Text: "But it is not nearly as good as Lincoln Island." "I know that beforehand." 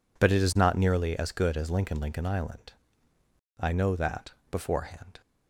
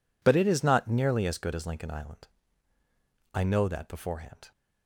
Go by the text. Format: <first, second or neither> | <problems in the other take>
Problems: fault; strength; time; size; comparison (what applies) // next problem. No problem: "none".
second | says "Lincoln" twice; at 2.0 s // pauses between "that" and "beforehand"; slight; at 4.3 s; 0.18 s long